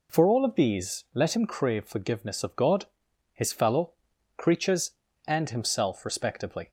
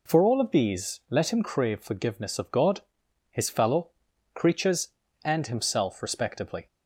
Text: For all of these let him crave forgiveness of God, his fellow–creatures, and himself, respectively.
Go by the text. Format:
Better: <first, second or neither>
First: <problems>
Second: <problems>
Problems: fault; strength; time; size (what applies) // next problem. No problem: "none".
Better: neither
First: none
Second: none